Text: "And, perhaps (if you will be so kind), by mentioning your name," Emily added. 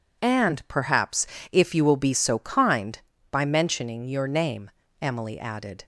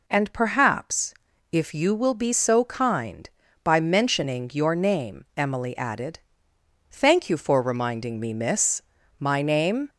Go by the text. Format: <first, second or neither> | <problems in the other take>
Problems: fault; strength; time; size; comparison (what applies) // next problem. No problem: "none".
first | goes on to say "Thank you for reminding me miss My name"; strong; from 6.9 s on; 2.9 s long